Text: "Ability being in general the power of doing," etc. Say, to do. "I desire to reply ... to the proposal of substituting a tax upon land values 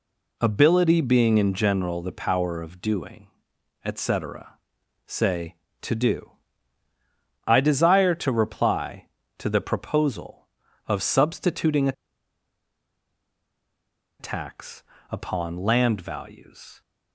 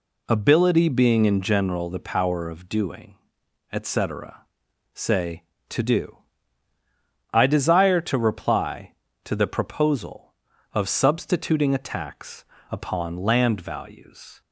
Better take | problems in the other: second | pauses between "a" and "tax"; strong; at 11.9 s; 2.2 s long // pauses between "tax" and "upon"; slight; at 14.8 s; 0.26 s long; slight in the second

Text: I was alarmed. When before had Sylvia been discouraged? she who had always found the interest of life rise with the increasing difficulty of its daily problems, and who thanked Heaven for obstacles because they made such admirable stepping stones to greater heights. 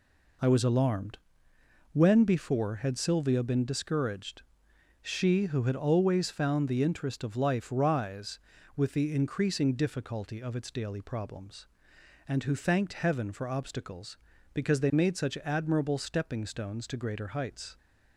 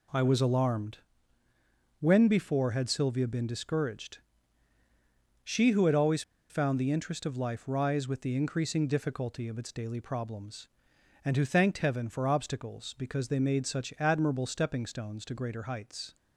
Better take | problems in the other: first | pauses between "always" and "found"; slight; at 6.2 s; 0.28 s long

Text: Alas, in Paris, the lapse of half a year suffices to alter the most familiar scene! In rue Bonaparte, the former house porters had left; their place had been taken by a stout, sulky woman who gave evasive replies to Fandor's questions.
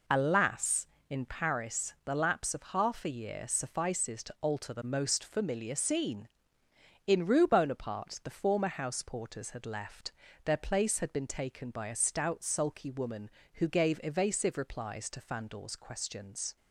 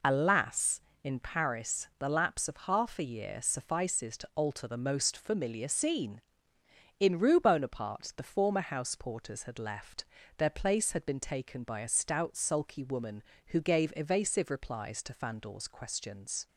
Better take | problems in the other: neither | none

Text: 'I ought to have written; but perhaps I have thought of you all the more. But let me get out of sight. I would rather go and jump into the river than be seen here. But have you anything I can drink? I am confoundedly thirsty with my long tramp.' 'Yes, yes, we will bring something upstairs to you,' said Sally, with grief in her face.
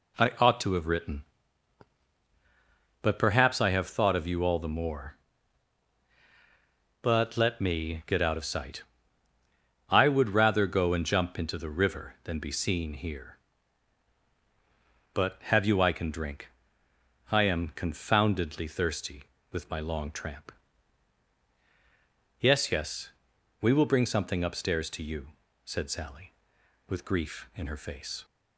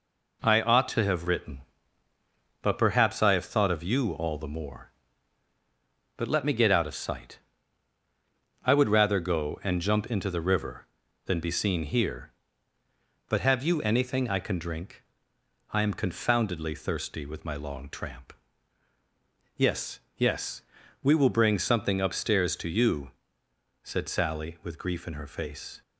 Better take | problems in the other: second | skips "anything"; at 15.8 s

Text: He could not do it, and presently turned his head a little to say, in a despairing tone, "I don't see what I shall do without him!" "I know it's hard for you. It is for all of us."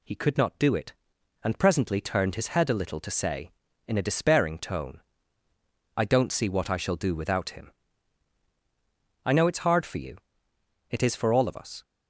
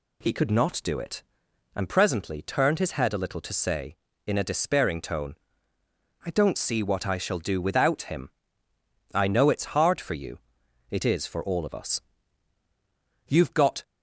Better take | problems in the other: first | goes on to say "You've got"; from 13.2 s on; 0.56 s long

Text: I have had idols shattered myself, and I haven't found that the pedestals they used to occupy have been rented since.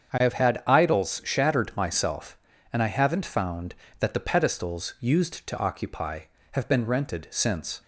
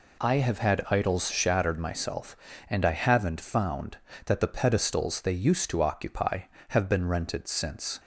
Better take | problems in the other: second | starts louder than the rest; strong; until 1.2 s; 7 dB // skips "they"; at 4.9 s

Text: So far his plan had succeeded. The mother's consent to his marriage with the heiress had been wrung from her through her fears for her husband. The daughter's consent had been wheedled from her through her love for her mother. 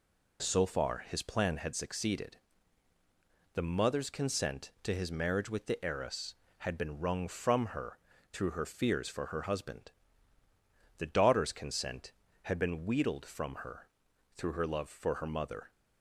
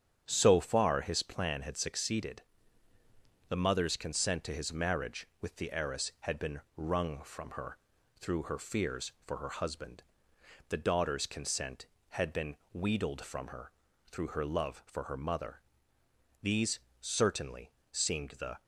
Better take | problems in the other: first | starts louder than the rest; strong; until 1.2 s; 8.5 dB // pauses between "been" and "wrung"; slight; at 6.6 s; 0.16 s long // pauses between "her" and "through"; at 7.7 s; 0.42 s long; slight in the first // pauses between "been" and "wheedled"; slight; at 12.5 s; 0.18 s long // pauses between "her" and "through"; at 13.7 s; 0.40 s long; noticeable in the first // goes on to say "These certainly seemed the"; strong; from 16.4 s on; 2.2 s long

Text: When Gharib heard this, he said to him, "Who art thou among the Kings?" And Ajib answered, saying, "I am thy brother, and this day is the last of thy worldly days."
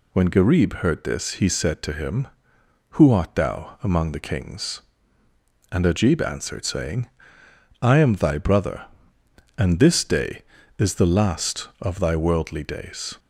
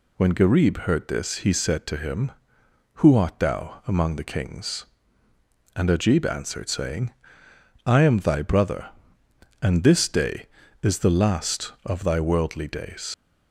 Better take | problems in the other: first | leaves "days" unfinished; at 13.1 s; 85 ms

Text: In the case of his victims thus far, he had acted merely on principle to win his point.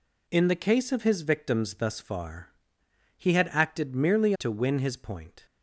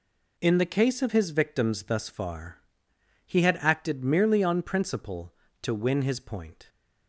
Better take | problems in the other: second | skips "on principle"; at 4.3 s

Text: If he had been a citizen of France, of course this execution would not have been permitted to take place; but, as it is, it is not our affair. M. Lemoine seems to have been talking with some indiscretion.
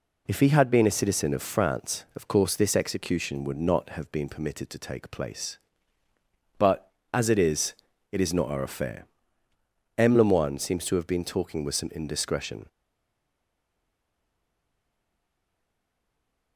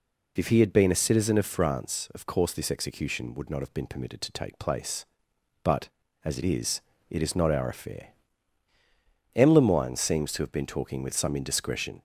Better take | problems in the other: second | stays silent after the last word; strong; from 12.6 s on; 3.9 s long

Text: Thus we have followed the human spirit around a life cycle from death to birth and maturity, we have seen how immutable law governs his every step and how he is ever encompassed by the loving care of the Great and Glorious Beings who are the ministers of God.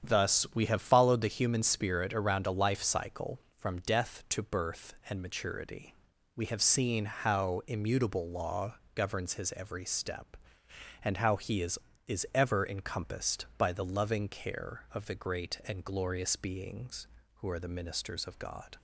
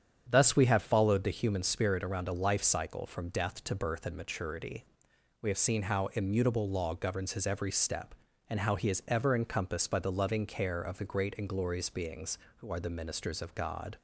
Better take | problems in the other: second | starts louder than the rest; strong; until 1.1 s; 8.5 dB; strong in the second // pauses between "law" and "governs"; slight; at 8.7 s; 0.22 s long // says "is" twice; at 12.0 s

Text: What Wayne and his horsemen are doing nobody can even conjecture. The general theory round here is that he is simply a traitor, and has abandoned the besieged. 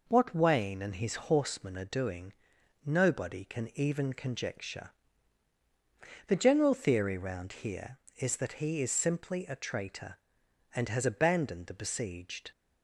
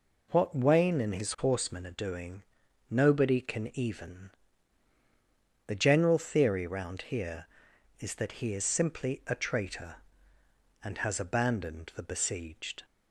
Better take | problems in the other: first | pauses between "doing" and "nobody"; noticeable; at 2.4 s; 0.46 s long; noticeable in the first // skips "conjecture"; at 4.9 s

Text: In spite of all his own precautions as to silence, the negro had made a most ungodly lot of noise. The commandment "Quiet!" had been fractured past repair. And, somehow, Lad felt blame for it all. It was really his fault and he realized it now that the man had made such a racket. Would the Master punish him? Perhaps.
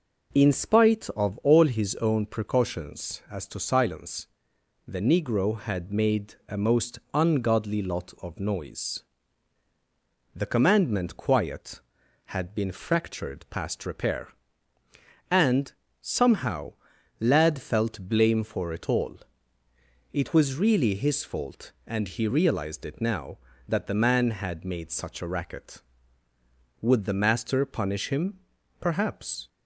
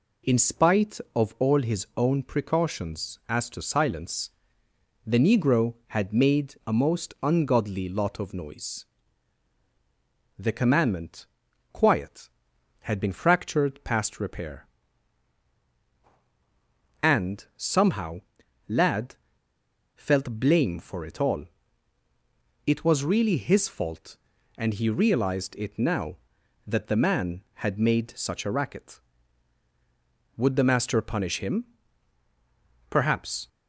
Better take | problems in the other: first | pauses between "commandment" and "Quiet"; noticeable; at 11.2 s; 0.48 s long // pauses between "Lad" and "felt"; noticeable; at 19.1 s; 0.79 s long

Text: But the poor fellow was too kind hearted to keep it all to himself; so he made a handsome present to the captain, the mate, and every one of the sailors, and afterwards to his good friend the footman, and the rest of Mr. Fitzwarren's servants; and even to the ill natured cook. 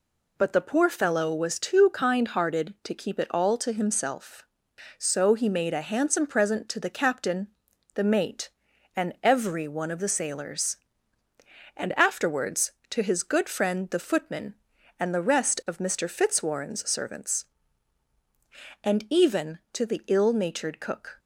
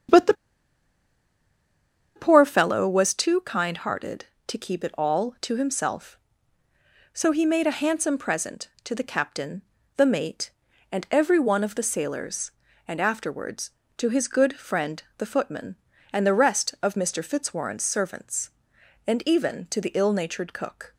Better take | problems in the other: first | starts louder than the rest; strong; until 2.9 s; 8 dB // pauses between "the" and "poor"; strong; at 0.3 s; 1.8 s long // pauses between "friend" and "the"; slight; at 15.0 s; 0.16 s long

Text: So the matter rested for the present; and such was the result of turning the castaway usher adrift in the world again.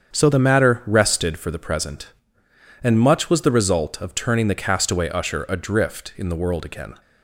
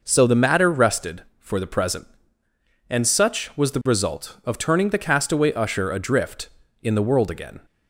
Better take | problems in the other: second | starts louder than the rest; strong; until 1.1 s; 7.5 dB // says "much" for "such"; at 2.9 s

